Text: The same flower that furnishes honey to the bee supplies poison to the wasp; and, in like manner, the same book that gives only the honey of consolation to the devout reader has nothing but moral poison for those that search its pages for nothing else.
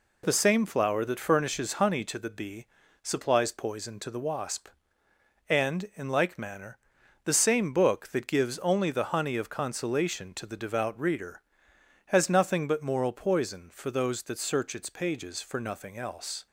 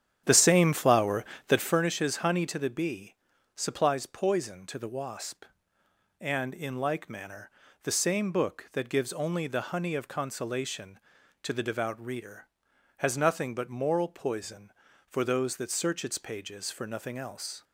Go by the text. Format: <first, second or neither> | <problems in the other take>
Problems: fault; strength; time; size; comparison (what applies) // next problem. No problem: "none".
first | starts louder than the rest; strong; until 1.8 s; 10 dB // pauses between "bee" and "supplies"; at 3.1 s; 0.40 s long; also in the first